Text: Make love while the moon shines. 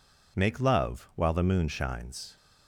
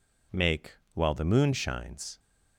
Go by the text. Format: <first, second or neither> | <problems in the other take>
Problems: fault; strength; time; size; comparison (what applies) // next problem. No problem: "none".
first | skips "love"; at 0.8 s